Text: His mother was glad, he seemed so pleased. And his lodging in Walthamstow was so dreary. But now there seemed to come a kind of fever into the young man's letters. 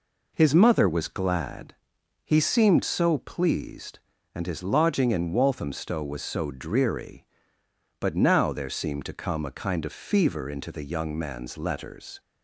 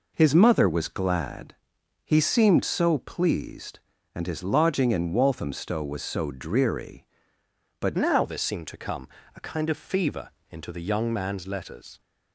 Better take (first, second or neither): first